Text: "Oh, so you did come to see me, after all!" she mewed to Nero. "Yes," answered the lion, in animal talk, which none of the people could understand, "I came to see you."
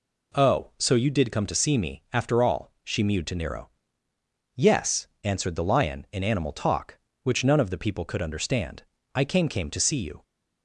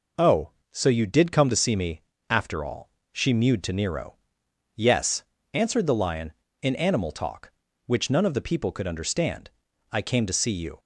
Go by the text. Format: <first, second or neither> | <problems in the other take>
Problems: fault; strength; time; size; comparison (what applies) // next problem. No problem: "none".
second | says "came" twice; at 9.4 s